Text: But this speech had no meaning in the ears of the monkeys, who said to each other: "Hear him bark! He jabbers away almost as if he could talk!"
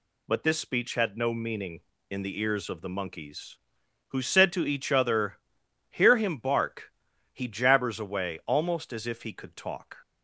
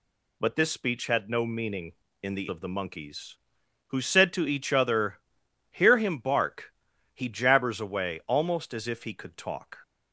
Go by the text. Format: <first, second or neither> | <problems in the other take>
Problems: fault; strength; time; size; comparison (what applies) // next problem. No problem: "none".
first | skips "ears"; at 2.4 s